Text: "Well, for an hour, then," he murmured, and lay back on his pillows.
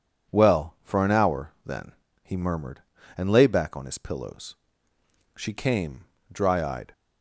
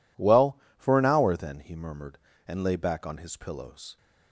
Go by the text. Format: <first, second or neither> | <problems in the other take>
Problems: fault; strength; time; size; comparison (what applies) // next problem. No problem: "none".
second | goes on to say "She came dry eyed"; from 5.3 s on; 1.5 s long